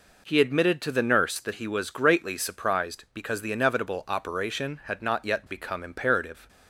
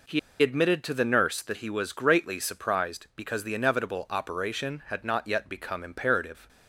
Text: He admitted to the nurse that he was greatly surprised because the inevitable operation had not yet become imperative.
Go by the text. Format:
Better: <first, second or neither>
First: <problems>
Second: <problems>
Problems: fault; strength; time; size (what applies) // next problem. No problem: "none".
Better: first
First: none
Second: pauses between "He" and "admitted"; slight; at 0.1 s; 0.22 s long